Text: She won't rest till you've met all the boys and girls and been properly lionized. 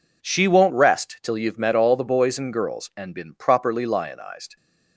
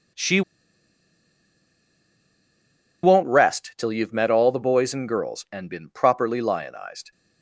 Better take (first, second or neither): first